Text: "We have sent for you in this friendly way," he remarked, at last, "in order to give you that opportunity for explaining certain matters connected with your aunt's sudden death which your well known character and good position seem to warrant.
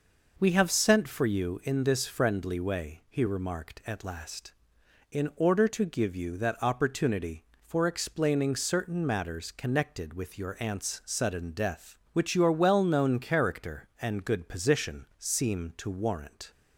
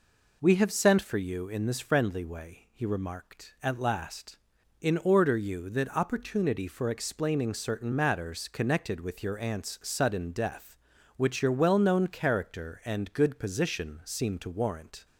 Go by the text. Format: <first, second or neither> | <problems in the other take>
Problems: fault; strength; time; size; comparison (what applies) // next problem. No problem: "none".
first | skips "to give"; at 5.3 s